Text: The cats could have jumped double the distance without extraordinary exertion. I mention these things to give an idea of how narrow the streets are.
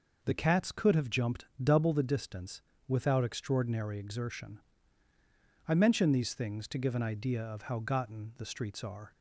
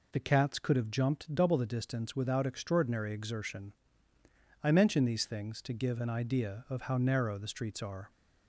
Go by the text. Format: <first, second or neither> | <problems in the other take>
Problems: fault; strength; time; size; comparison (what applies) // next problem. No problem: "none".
second | pauses between "jumped" and "double"; slight; at 1.4 s; 0.16 s long // pauses between "distance" and "without"; slight; at 2.6 s; 0.26 s long // says "gotten" for "narrow"; at 7.7 s